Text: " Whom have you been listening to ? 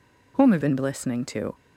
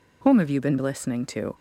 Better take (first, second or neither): second